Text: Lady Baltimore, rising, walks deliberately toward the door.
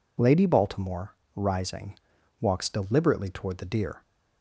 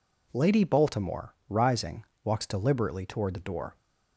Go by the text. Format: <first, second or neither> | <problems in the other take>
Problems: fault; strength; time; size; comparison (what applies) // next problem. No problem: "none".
second | says "deer" for "door"; at 3.6 s